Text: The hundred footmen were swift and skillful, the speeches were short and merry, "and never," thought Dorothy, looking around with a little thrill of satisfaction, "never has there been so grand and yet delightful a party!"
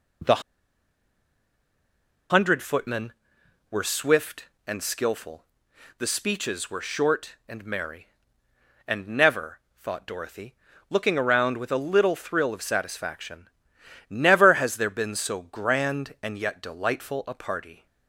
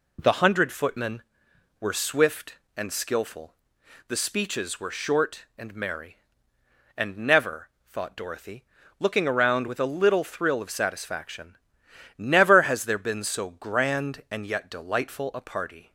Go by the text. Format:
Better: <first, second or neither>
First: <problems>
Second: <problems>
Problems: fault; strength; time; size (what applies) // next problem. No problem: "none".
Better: second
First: pauses between "The" and "hundred"; strong; at 0.4 s; 1.8 s long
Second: none